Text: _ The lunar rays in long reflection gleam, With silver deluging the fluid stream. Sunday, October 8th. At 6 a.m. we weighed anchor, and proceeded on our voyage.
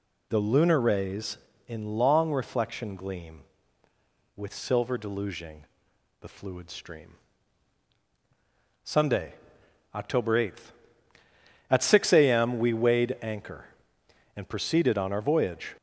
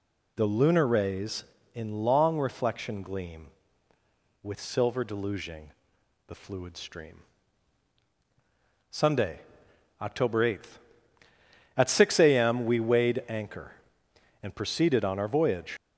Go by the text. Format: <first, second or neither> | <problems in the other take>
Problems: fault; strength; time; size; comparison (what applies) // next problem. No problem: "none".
first | pauses between "deluging" and "the"; noticeable; at 5.7 s; 0.56 s long; noticeable in the first // leaves "voyage" unfinished; at 15.7 s; 60 ms